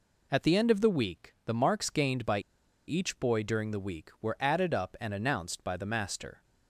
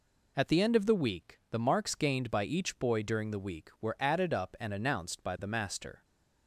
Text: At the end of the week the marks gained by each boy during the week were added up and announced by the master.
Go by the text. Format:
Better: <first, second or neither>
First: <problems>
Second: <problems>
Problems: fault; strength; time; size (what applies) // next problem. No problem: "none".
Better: second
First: pauses between "by" and "each"; noticeable; at 2.3 s; 0.48 s long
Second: none